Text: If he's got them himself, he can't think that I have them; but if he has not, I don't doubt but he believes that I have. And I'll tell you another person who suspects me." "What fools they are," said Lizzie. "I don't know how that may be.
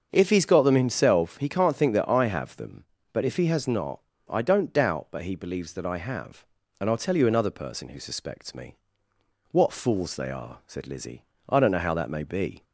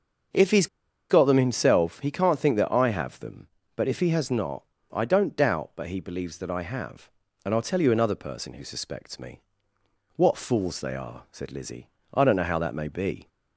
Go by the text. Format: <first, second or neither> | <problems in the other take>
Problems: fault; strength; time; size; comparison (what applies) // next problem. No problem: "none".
first | starts louder than the rest; until 1.7 s; 6.5 dB; also in the first // pauses between "he's" and "got"; at 0.6 s; 0.42 s long